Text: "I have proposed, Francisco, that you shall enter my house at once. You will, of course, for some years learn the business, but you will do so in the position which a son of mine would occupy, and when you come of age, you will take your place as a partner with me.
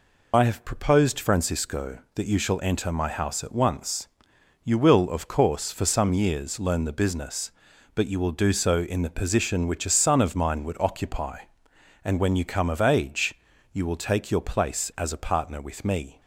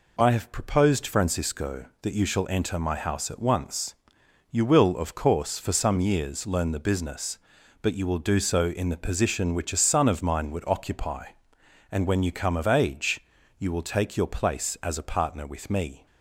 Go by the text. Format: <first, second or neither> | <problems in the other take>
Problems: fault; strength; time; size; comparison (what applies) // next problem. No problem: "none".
second | loses the start of "I"; at 0.3 s; 20 ms